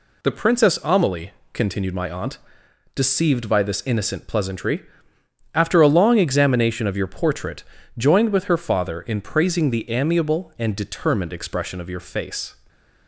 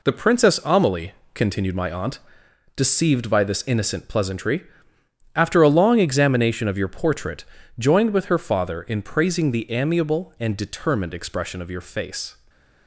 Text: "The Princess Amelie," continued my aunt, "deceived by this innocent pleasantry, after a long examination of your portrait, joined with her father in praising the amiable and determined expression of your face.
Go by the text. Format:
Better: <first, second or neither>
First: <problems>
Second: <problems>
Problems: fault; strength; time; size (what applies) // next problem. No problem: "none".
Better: first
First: none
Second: gets quieter; strong; throughout; 7.5 dB // stays silent after the last word; slight; from 12.3 s on; 0.5 s long